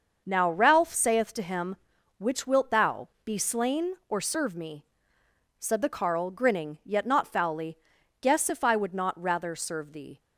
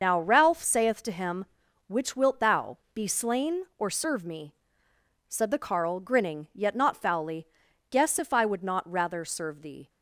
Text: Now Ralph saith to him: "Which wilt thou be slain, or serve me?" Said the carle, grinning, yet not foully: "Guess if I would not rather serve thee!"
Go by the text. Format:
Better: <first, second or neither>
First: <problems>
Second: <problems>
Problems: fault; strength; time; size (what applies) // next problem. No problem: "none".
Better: first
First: starts louder than the rest; until 1.2 s; 6.5 dB // pauses between "thou" and "be"; slight; at 3.0 s; 0.16 s long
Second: loses the start of "Now"; at 0.0 s; 60 ms // starts louder than the rest; until 1.0 s; 6.5 dB // pauses between "thou" and "be"; slight; at 2.7 s; 0.16 s long